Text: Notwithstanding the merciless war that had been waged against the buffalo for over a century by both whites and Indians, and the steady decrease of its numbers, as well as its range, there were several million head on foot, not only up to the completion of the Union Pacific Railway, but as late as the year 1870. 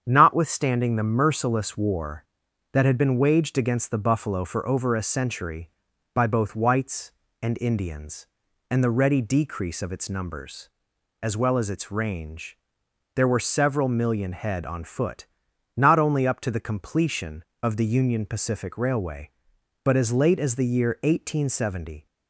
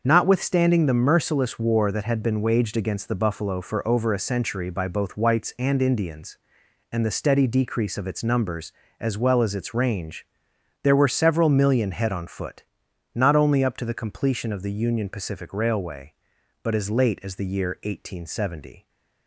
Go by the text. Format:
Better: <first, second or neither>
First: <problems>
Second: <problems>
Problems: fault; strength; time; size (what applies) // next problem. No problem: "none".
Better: second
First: starts louder than the rest; strong; until 1.0 s; 8 dB // says "ready" for "steady"; at 8.8 s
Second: starts louder than the rest; until 1.0 s; 6 dB